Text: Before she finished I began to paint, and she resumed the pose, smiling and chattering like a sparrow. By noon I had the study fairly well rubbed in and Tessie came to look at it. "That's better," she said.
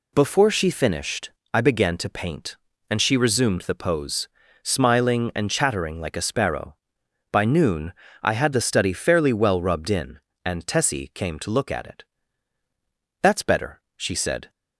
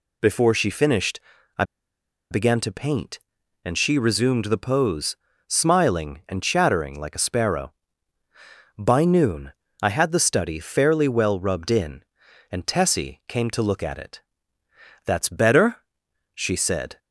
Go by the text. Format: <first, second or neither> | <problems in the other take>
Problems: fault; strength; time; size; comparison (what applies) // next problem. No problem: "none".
first | pauses between "finished" and "I"; at 1.1 s; 0.38 s long; slight in the first // pauses between "I" and "began"; noticeable; at 1.6 s; 0.67 s long // pauses between "noon" and "I"; slight; at 9.5 s; 0.28 s long; slight in the first